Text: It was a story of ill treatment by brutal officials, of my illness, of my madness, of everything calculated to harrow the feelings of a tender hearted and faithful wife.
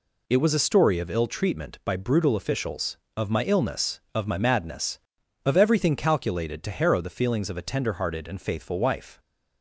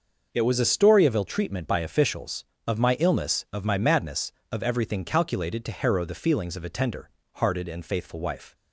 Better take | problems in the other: first | skips "brutal"; at 1.8 s // pauses between "tender" and "hearted"; slight; at 7.1 s; 0.24 s long

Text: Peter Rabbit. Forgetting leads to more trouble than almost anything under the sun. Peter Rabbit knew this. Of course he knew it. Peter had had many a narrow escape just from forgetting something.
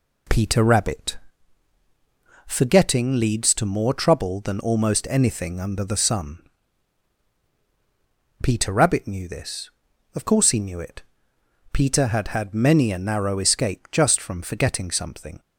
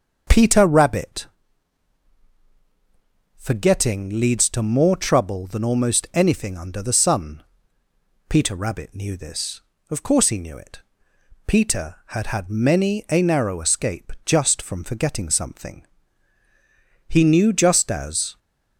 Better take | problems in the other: first | starts louder than the rest; until 3.3 s; 6.5 dB // goes on to say "He knew just as"; noticeable; from 17.1 s on; 1.2 s long

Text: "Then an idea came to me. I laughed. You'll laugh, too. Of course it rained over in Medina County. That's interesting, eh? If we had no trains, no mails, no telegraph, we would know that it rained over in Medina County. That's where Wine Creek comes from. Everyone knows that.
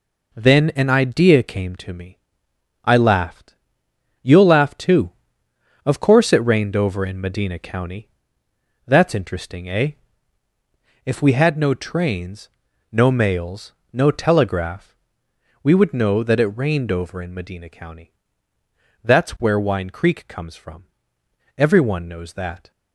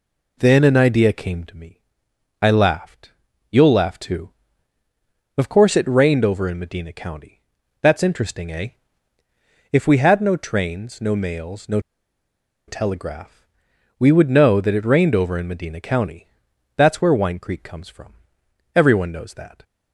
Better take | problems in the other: first | pauses between "no" and "telegraph"; noticeable; at 11.7 s; 0.88 s long

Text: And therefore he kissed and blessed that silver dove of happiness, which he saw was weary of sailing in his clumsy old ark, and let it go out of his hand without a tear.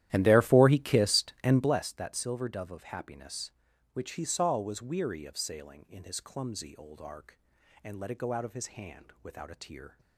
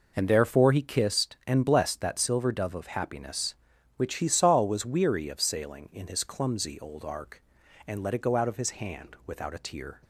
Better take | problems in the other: second | starts louder than the rest; strong; until 1.8 s; 12.5 dB

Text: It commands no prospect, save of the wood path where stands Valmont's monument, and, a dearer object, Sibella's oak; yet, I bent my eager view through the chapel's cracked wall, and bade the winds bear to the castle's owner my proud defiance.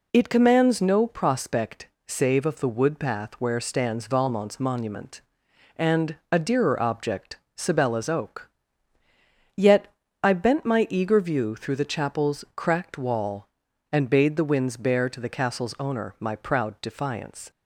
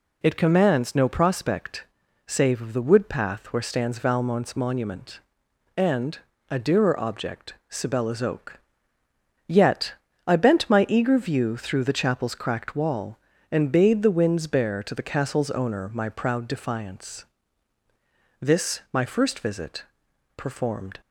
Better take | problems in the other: first | goes on to say "This my first visit performed"; strong; from 18.3 s on; 2.6 s long

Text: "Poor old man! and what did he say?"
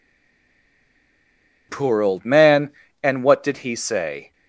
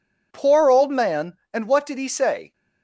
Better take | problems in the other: second | stays silent before the first word; noticeable; until 1.6 s; 1.6 s long

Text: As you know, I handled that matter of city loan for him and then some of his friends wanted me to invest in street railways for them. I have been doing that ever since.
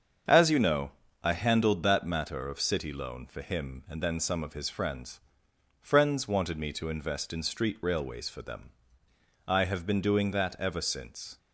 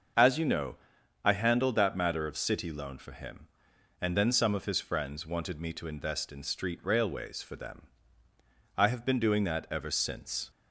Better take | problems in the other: second | starts louder than the rest; strong; until 1.6 s; 7.5 dB; also in the second // says "friends" twice; at 5.7 s

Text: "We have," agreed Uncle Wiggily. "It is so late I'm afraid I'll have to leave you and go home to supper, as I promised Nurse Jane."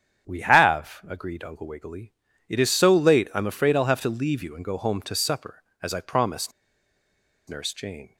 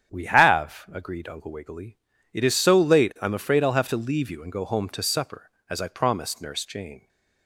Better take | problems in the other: second | starts louder than the rest; strong; until 1.3 s; 9 dB; strong in the second // pauses between "promised" and "Nurse"; at 6.5 s; 0.98 s long

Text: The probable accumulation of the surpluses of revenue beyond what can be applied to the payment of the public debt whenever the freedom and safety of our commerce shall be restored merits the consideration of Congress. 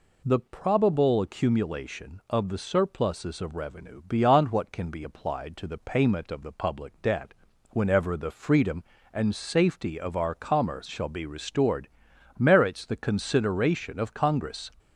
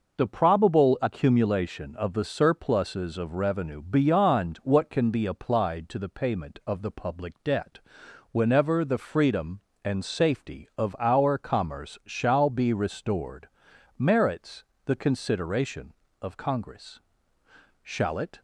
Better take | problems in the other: first | pauses between "debt" and "whenever"; noticeable; at 7.7 s; 0.54 s long; also in the first // pauses between "restored" and "merits"; noticeable; at 13.4 s; 0.50 s long; noticeable in the first // pauses between "merits" and "the"; slight; at 14.6 s; 0.20 s long // goes on to say "Shall it"; from 17.8 s on; 0.56 s long

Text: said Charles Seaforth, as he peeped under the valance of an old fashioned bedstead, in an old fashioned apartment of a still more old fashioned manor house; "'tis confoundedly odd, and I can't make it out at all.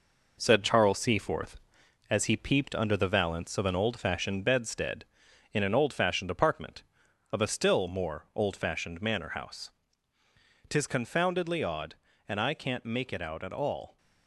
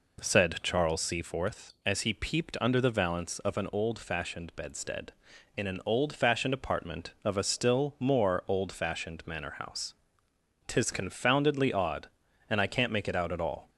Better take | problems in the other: second | gets quieter; noticeable; throughout; 5.5 dB

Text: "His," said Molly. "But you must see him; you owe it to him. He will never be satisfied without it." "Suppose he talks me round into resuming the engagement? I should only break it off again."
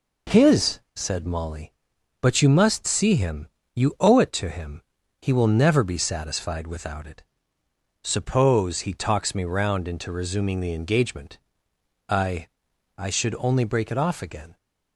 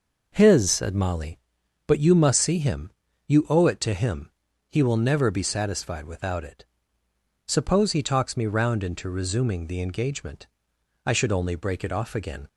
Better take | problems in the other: second | says "I" twice; at 12.9 s

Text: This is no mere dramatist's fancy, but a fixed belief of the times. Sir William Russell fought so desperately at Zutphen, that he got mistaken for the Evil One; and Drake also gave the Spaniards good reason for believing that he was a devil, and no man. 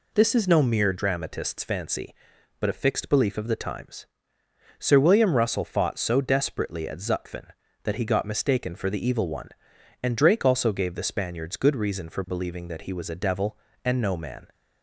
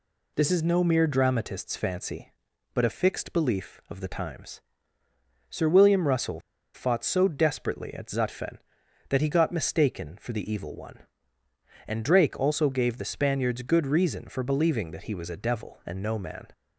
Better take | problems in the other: first | pauses between "Russell" and "fought"; slight; at 6.3 s; 0.34 s long

